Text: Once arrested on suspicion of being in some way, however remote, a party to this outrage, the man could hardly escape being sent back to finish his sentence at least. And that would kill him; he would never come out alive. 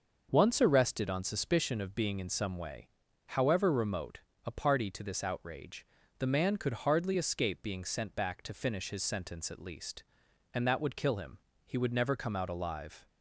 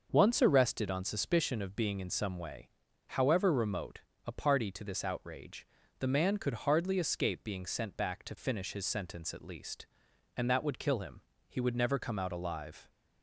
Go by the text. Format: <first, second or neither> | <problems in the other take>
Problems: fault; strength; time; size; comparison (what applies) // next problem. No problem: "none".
neither | starts louder than the rest; the same in both